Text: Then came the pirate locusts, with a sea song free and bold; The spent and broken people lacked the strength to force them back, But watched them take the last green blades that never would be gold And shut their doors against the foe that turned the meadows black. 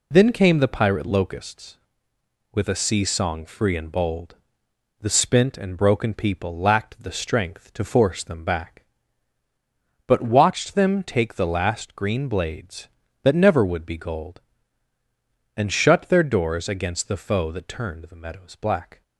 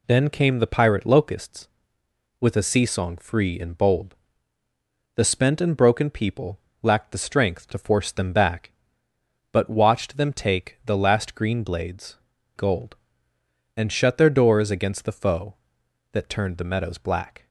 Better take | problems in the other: first | pauses between "people" and "lacked"; slight; at 6.5 s; 0.22 s long // skips "that never would be"; at 12.3 s

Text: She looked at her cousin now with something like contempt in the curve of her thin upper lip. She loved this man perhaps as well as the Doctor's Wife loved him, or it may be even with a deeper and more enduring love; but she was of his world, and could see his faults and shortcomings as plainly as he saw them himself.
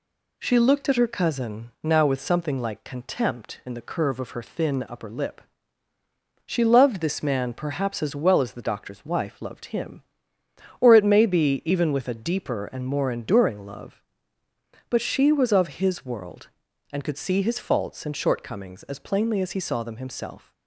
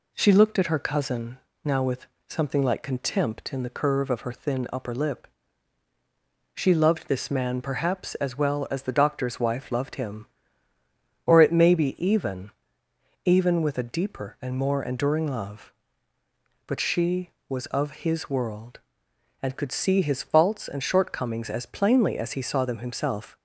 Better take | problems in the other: first | pauses between "cousin" and "now"; slight; at 1.3 s; 0.26 s long // pauses between "with" and "something"; slight; at 2.0 s; 0.22 s long // says "even" twice; at 13.2 s

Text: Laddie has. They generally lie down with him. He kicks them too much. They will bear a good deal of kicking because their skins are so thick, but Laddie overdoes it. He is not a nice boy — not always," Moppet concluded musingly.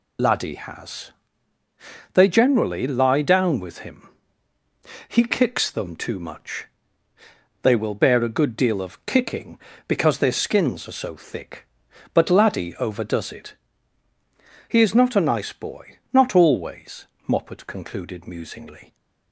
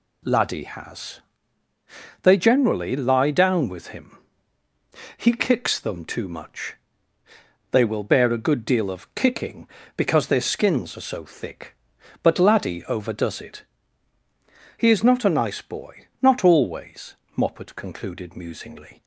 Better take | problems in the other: second | loses the start of "Laddie"; at 0.1 s; 35 ms

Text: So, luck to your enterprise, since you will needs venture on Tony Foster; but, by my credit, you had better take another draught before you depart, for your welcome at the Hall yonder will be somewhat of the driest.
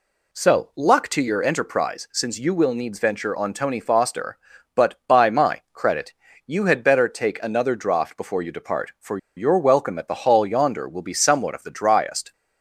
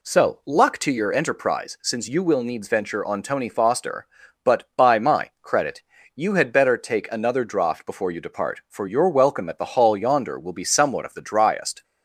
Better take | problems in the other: second | pauses between "for" and "your"; slight; at 9.1 s; 0.19 s long

